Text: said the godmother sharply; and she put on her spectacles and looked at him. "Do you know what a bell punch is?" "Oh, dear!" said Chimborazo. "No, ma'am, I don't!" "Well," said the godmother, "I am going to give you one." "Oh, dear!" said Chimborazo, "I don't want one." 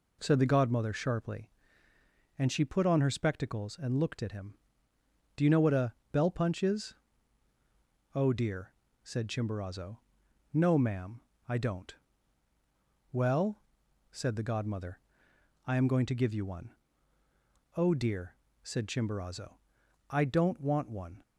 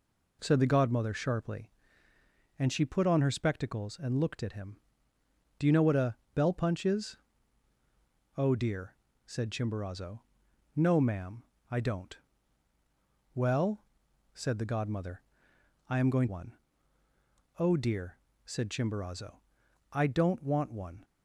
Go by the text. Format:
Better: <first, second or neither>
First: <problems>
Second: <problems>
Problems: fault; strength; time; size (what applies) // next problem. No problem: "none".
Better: first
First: pauses between "a" and "bell"; slight; at 5.9 s; 0.18 s long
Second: pauses between "a" and "bell"; slight; at 6.1 s; 0.18 s long // skips "to give you"; at 16.2 s